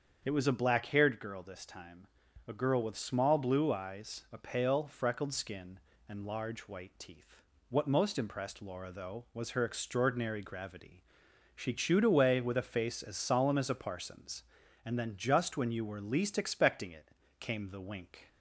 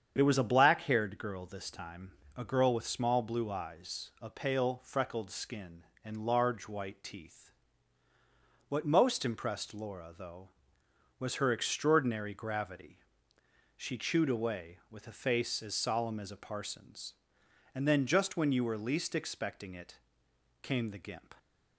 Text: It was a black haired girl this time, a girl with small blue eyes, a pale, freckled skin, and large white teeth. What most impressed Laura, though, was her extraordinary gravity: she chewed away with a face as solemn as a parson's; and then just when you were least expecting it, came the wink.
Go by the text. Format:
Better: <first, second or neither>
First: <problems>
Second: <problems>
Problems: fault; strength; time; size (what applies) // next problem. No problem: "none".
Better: first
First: starts louder than the rest; strong; until 1.2 s; 7 dB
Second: starts louder than the rest; strong; until 1.1 s; 8 dB // says "gimp" for "wink"; at 21.0 s